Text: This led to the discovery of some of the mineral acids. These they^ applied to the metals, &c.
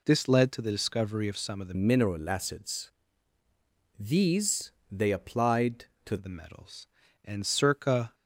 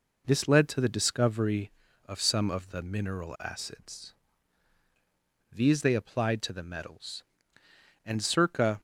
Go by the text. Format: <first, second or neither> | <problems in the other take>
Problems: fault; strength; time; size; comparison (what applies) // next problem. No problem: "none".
second | changes voice from "mineral" to "to"; from 1.7 to 6.1 s; 4.4 s long // pauses between "These" and "they"; slight; at 4.6 s; 0.22 s long